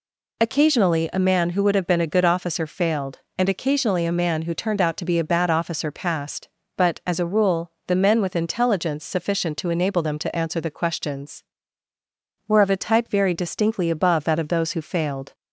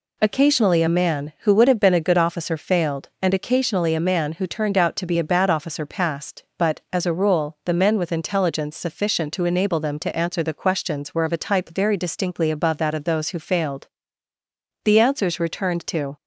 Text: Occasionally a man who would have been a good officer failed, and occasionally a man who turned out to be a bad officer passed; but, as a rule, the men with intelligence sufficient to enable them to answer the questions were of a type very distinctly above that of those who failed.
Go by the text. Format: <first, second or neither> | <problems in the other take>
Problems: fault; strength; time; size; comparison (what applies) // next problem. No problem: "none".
first | goes on to say "The answers returned to"; from 14.8 s on; 1.3 s long